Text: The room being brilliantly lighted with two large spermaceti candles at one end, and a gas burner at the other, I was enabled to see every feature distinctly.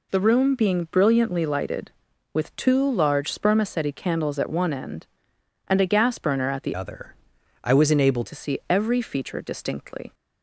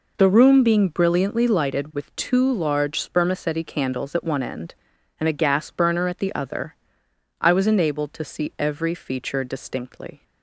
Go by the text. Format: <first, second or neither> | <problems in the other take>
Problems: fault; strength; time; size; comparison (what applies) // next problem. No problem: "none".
second | changes voice from "other" to "enabled"; from 6.7 to 8.2 s; 1.5 s long